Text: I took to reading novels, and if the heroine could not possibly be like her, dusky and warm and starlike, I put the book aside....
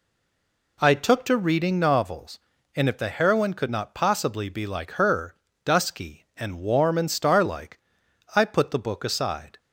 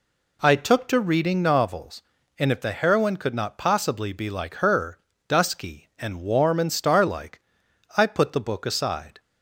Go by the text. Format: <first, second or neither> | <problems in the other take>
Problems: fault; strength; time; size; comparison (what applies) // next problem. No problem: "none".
second | stays silent before the first word; slight; until 0.7 s; 0.7 s long